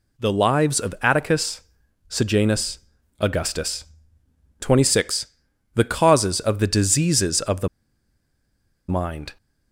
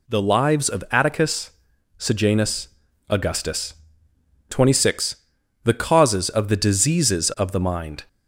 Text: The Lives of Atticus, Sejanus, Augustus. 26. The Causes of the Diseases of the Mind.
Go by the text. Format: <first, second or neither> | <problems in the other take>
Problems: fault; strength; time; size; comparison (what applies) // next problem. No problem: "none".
second | pauses between "the" and "Mind"; at 7.6 s; 1.2 s long